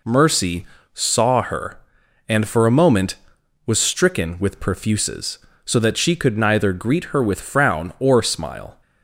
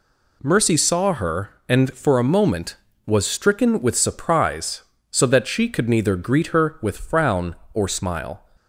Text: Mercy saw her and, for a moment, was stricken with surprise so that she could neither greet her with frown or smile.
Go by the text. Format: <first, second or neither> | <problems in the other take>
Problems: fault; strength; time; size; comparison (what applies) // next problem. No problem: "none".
second | pauses between "Mercy" and "saw"; slight; at 0.6 s; 0.30 s long // says "perfuses" for "surprise"; at 4.6 s